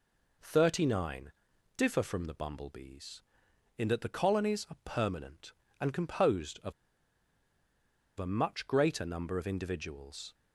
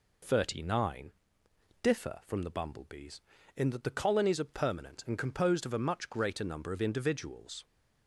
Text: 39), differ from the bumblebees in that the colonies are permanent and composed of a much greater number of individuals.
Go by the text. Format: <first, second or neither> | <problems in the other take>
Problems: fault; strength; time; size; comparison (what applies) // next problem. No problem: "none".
second | pauses between "of" and "a"; strong; at 6.7 s; 1.4 s long